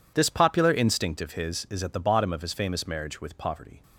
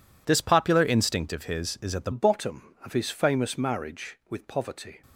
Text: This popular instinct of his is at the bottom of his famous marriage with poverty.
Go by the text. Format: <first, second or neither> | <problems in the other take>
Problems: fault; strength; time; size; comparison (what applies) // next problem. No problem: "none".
first | changes voice at "bottom"; from 2.1 s on; 2.9 s long